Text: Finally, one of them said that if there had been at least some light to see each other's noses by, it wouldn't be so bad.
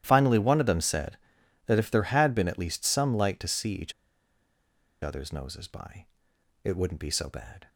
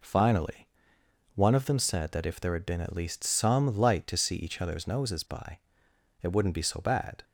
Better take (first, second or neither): second